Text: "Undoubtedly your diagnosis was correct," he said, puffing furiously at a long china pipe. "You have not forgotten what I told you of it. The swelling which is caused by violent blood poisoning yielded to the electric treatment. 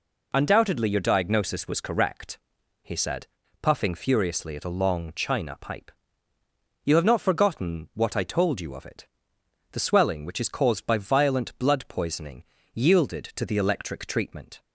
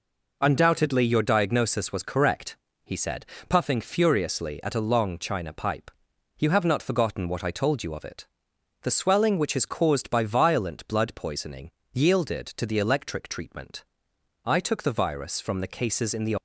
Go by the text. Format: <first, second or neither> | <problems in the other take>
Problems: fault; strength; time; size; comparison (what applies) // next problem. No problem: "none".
first | pauses between "poisoning" and "yielded"; slight; at 11.6 s; 0.24 s long; slight in the first // goes on to say "I took the virus from the cases in the"; strong; from 14.4 s on; 1.9 s long